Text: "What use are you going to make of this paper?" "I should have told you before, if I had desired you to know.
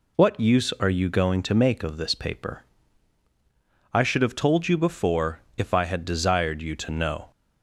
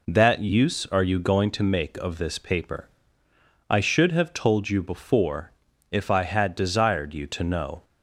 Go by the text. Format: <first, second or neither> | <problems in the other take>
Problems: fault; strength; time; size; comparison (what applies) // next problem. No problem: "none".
first | says "That" for "What"; at 0.0 s